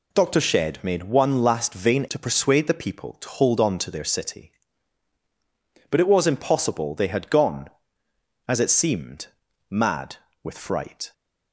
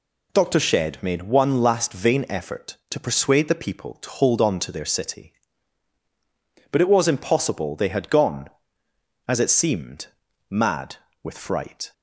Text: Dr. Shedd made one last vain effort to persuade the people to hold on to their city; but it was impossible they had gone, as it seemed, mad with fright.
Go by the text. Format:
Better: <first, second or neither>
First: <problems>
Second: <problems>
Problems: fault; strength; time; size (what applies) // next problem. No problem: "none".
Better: second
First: skips "effort"; at 2.0 s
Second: none